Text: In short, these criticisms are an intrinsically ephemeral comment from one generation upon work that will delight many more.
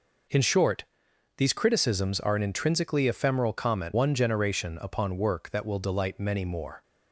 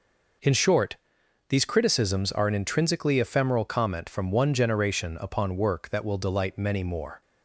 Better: second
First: skips "from"; at 3.9 s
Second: none

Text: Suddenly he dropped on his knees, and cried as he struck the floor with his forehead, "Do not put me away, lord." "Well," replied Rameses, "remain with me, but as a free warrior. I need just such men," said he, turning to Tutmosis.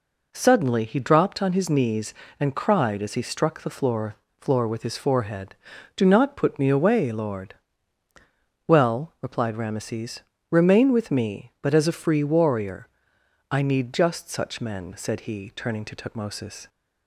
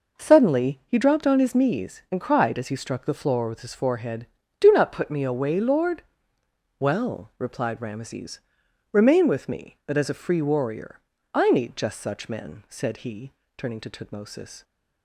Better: second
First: says "floor" twice; at 4.4 s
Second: none

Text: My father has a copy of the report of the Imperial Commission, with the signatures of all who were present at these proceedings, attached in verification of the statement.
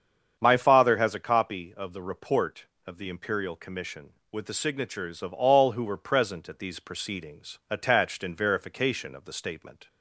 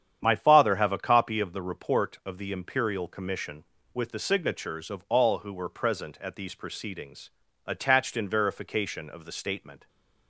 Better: first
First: starts louder than the rest; strong; until 1.3 s; 7.5 dB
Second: starts louder than the rest; strong; until 1.2 s; 9 dB // says "have" for "has"; at 0.7 s

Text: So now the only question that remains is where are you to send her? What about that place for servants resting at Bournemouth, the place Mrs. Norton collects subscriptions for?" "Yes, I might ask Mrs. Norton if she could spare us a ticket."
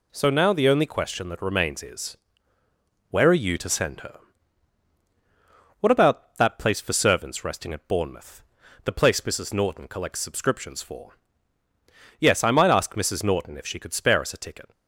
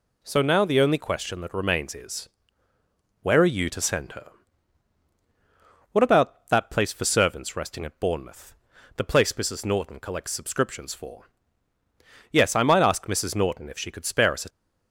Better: first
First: pauses between "is" and "where"; noticeable; at 2.1 s; 0.94 s long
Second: pauses between "is" and "where"; noticeable; at 2.2 s; 0.94 s long // stops before "ticket"; at 14.4 s

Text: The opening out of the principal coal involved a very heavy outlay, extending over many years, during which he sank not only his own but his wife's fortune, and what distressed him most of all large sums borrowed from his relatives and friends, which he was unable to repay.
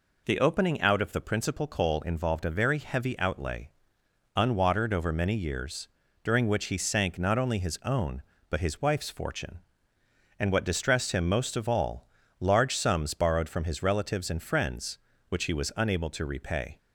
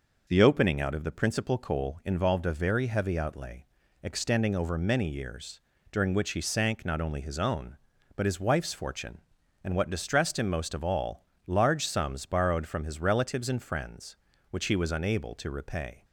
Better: second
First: says "unwatered" for "extending"; at 4.3 s // pauses between "all" and "large"; slight; at 12.0 s; 0.34 s long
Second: pauses between "all" and "large"; slight; at 11.2 s; 0.22 s long

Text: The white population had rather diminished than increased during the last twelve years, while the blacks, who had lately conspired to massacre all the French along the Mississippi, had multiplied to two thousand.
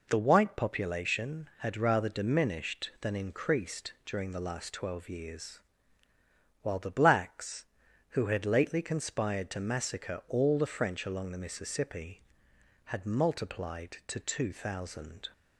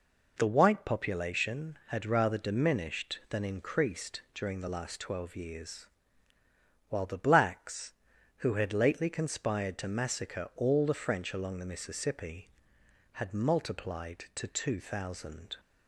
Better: neither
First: none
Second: none

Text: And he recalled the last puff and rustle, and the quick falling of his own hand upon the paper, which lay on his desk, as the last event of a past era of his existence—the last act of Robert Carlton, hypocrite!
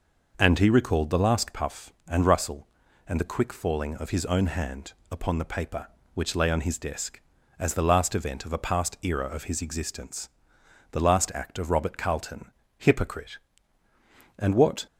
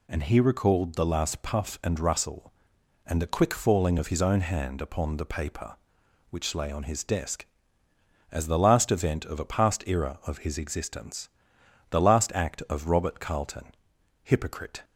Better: second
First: pauses between "hand" and "upon"; slight; at 4.9 s; 0.18 s long // goes on to say "And what"; slight; from 14.3 s on; 0.48 s long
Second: none

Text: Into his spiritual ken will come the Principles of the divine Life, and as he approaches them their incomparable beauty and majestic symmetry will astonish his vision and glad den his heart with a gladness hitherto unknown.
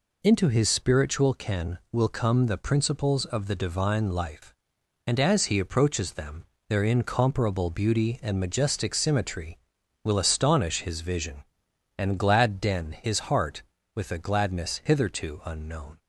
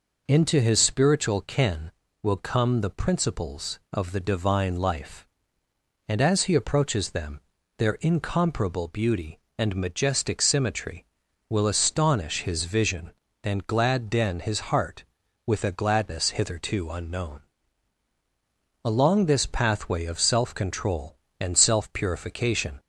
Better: first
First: pauses between "them" and "their"; slight; at 6.4 s; 0.24 s long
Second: pauses between "them" and "their"; slight; at 7.4 s; 0.36 s long // goes on to say "Along this pathway of self control and self purification"; strong; from 18.8 s on; 3.9 s long

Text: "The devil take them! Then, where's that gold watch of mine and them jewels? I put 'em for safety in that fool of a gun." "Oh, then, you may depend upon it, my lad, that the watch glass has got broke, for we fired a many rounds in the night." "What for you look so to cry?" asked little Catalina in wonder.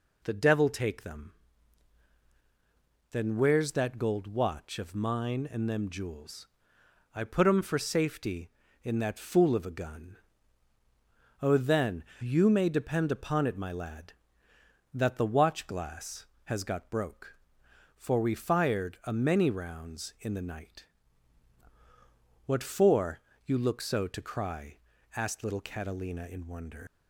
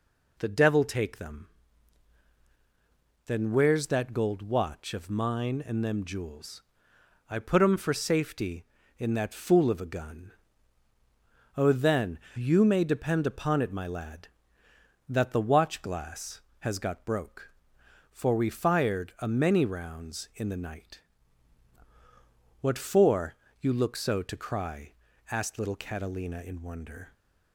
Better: second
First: pauses between "for" and "you"; slight; at 23.1 s; 0.26 s long // leaves "wonder" unfinished; at 26.8 s; 110 ms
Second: pauses between "for" and "you"; slight; at 23.3 s; 0.26 s long

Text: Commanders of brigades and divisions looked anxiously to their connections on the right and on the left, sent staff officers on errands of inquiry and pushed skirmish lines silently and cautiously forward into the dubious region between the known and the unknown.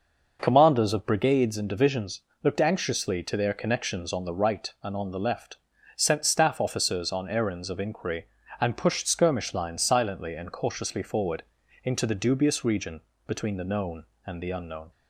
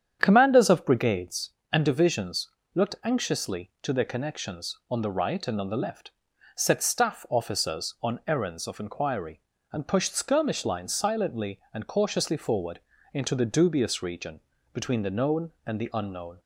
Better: first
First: pauses between "divisions" and "looked"; slight; at 2.2 s; 0.20 s long // pauses between "forward" and "into"; at 11.4 s; 0.42 s long // pauses between "region" and "between"; slight; at 13.0 s; 0.26 s long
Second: starts louder than the rest; strong; until 1.2 s; 8.5 dB // pauses between "divisions" and "looked"; slight; at 2.5 s; 0.24 s long // says "set" for "sent"; at 6.5 s // pauses between "forward" and "into"; slight; at 12.8 s; 0.34 s long // pauses between "region" and "between"; slight; at 14.4 s; 0.34 s long

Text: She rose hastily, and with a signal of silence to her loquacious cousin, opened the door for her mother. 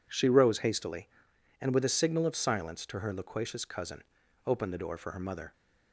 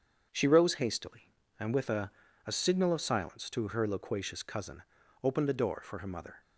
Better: first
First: none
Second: starts louder than the rest; strong; until 1.3 s; 7 dB // says "a" twice; at 2.4 s

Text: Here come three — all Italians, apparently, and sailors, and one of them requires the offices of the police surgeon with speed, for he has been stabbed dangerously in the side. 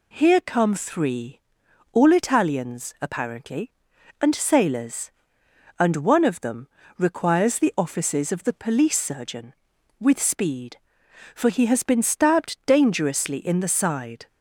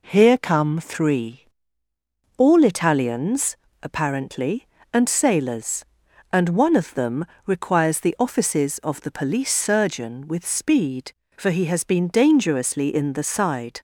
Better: first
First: pauses between "them" and "requires"; slight; at 6.6 s; 0.32 s long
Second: pauses between "them" and "requires"; slight; at 7.2 s; 0.22 s long // skips "stabbed"; at 12.0 s

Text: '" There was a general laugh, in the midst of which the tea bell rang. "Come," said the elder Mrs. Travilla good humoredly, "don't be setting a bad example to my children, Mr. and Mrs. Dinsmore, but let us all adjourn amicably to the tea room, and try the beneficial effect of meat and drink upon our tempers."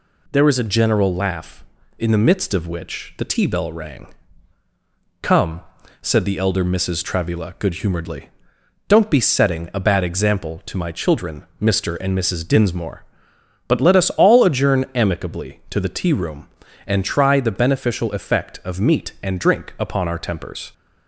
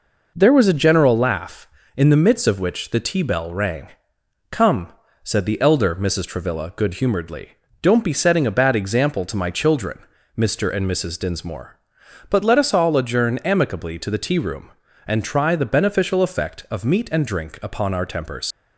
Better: first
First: none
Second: leaves "tempers" unfinished; at 18.5 s; 80 ms

